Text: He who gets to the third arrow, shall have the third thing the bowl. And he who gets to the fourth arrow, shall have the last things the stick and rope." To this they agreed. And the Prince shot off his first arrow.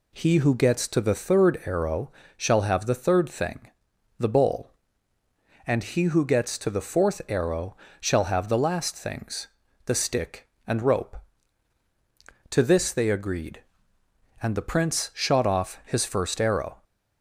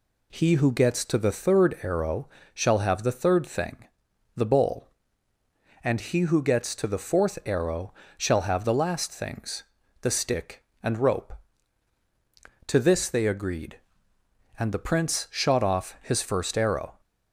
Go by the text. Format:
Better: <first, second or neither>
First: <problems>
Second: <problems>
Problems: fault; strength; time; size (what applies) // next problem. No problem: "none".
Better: neither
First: pauses between "thing" and "the"; noticeable; at 3.7 s; 0.48 s long // pauses between "things" and "the"; at 9.4 s; 0.38 s long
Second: pauses between "thing" and "the"; noticeable; at 3.8 s; 0.48 s long // pauses between "things" and "the"; at 9.6 s; 0.38 s long